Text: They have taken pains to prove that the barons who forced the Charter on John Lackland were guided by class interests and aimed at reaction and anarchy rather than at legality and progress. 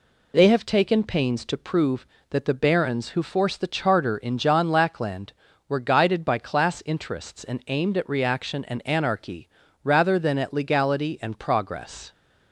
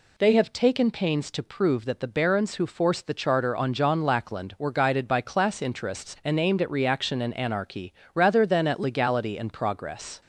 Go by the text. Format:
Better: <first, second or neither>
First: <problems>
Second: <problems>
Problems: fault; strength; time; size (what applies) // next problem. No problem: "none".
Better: second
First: says "in" for "on"; at 4.1 s // pauses between "anarchy" and "rather"; at 9.4 s; 0.38 s long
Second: pauses between "anarchy" and "rather"; slight; at 7.9 s; 0.22 s long